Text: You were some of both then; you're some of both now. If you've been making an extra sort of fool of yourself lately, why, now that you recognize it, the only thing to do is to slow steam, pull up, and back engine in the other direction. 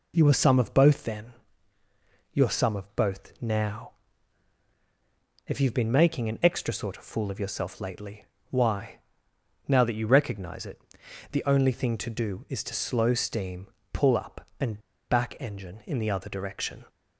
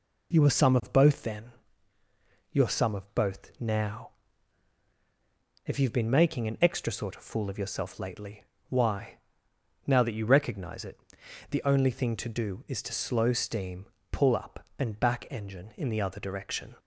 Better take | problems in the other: second | pauses between "and" and "back"; slight; at 14.7 s; 0.30 s long

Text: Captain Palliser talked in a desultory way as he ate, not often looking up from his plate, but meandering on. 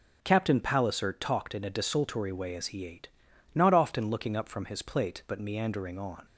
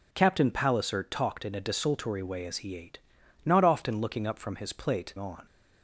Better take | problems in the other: first | skips "but meandering"; at 5.1 s

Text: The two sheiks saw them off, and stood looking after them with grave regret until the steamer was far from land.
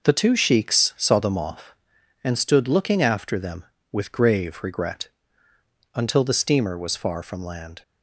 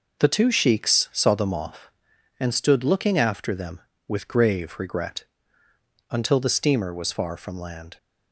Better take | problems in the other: neither | pauses between "regret" and "until"; noticeable; the same in both

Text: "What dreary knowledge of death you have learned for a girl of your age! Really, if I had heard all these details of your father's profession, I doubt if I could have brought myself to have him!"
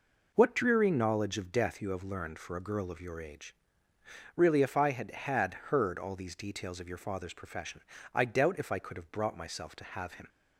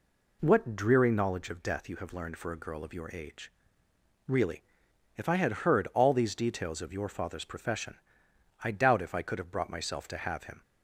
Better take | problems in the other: second | says "had" twice; at 5.1 s

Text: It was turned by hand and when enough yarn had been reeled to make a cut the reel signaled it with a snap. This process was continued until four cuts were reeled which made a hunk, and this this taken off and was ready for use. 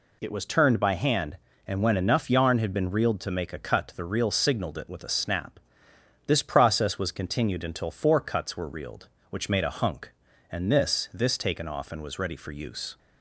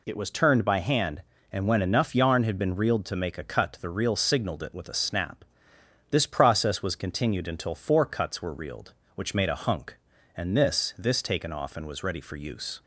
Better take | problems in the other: neither | none

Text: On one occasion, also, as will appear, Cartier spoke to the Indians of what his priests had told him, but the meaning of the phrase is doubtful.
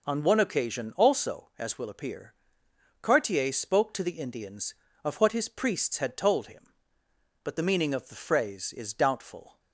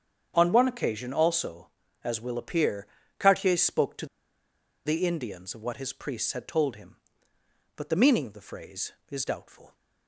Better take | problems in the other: first | starts louder than the rest; strong; until 1.3 s; 8 dB // pauses between "to" and "the"; noticeable; at 4.0 s; 0.80 s long

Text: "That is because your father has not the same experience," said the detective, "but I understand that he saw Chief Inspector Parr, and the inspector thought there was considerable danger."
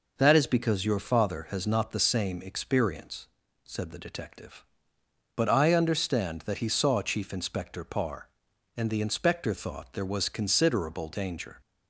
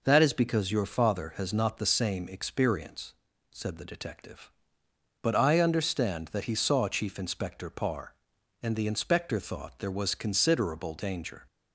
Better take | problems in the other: neither | none

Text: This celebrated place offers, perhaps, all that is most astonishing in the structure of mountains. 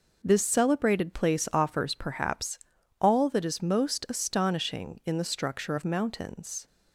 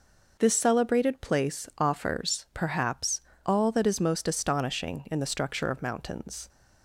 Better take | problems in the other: neither | none

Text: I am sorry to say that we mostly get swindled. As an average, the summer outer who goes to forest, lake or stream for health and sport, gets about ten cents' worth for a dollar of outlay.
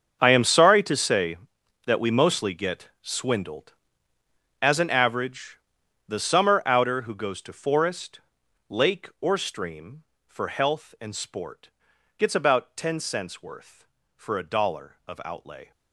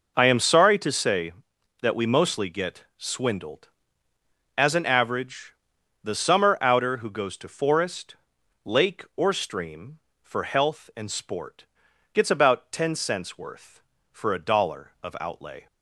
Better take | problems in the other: second | gets quieter; strong; throughout; 17.5 dB

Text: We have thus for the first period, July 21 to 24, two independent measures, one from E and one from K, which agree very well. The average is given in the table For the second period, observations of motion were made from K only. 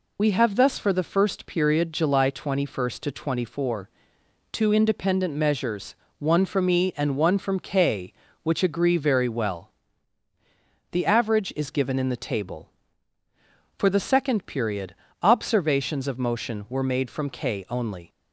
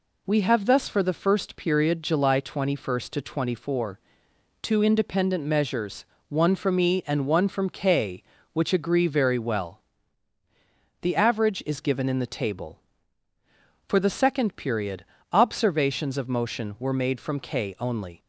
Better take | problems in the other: second | loses the start of "We"; at 0.1 s; 30 ms

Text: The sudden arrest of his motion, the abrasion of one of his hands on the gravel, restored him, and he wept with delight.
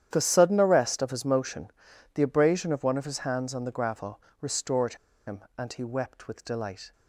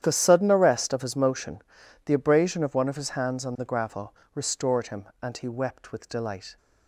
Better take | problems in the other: second | starts louder than the rest; strong; until 1.1 s; 10 dB; strong in the second // pauses between "restored" and "him"; slight; at 4.9 s; 0.31 s long

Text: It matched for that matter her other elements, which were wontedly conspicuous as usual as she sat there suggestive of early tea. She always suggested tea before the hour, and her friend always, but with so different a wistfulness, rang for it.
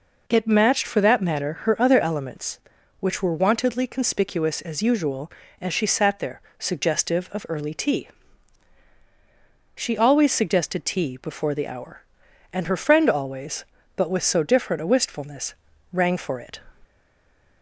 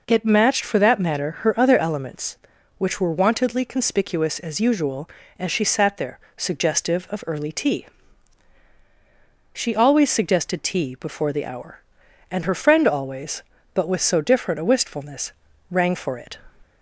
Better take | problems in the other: second | pauses between "there" and "suggestive"; slight; at 6.4 s; 0.18 s long; slight in the second // stays silent after the last word; slight; from 16.8 s on; 0.8 s long

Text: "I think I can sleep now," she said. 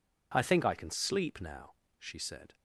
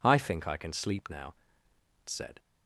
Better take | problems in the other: first | skips "she"; at 1.7 s

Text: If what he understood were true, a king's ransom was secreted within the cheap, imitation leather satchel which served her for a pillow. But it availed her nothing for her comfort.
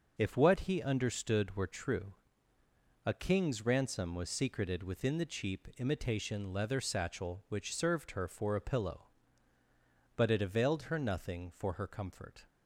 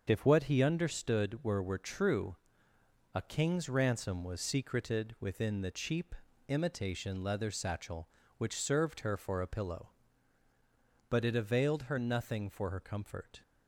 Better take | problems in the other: first | starts louder than the rest; until 1.0 s; 6.5 dB // says "were" twice; at 1.6 s

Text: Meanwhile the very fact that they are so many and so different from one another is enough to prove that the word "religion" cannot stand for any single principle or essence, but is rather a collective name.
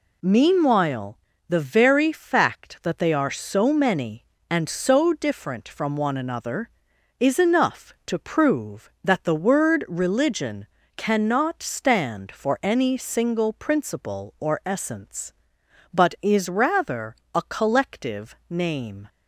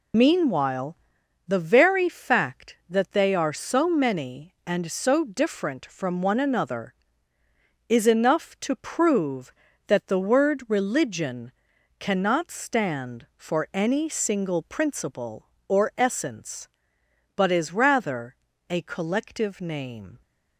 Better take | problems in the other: first | loses the start of "Meanwhile"; at 0.1 s; 85 ms // pauses between "Meanwhile" and "the"; noticeable; at 0.9 s; 0.50 s long; slight in the first // pauses between "religion" and "cannot"; noticeable; at 11.5 s; 0.48 s long; slight in the first // pauses between "rather" and "a"; slight; at 18.3 s; 0.36 s long; slight in the first

